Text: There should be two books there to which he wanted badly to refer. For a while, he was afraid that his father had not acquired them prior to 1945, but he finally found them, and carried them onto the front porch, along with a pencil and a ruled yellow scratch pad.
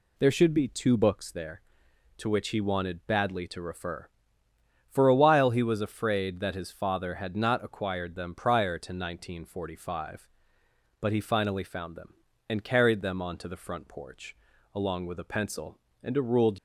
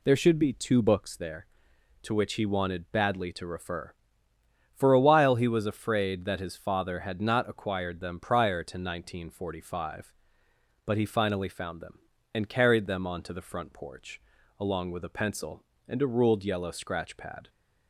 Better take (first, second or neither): second